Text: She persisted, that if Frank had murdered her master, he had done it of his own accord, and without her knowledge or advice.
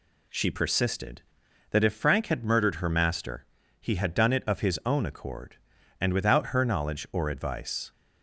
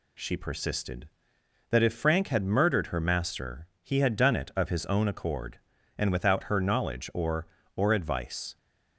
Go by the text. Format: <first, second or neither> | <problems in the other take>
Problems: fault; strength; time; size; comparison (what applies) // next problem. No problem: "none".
first | says "or" twice; at 7.7 s